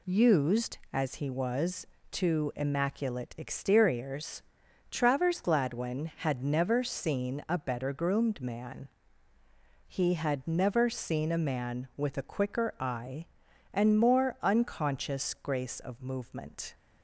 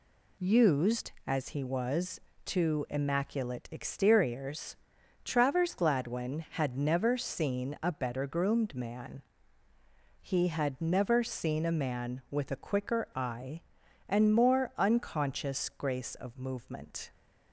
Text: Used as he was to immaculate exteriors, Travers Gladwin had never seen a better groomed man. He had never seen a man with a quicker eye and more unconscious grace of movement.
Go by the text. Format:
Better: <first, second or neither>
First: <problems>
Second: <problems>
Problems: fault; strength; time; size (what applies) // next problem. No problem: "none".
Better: neither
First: none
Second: none